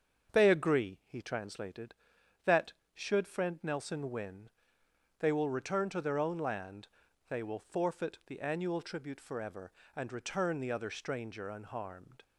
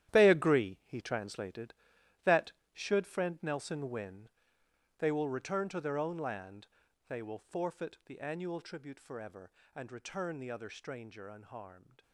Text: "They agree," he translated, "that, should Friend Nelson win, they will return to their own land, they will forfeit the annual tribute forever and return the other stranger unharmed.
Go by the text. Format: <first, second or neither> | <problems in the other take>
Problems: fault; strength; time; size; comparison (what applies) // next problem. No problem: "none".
first | gets quieter; strong; throughout; 12.5 dB // starts louder than the rest; strong; until 1.1 s; 11.5 dB; also in the first